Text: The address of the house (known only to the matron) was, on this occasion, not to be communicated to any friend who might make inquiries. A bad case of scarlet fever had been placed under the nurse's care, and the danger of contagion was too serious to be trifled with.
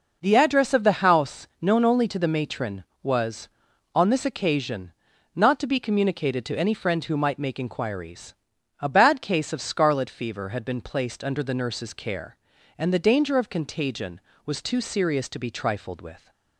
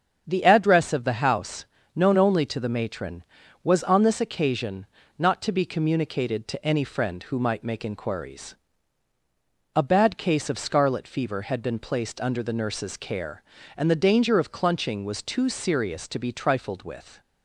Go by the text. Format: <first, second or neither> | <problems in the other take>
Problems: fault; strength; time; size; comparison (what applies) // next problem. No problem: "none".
first | starts louder than the rest; strong; until 1.2 s; 7 dB // says "clunching" for "contagion"; at 14.5 s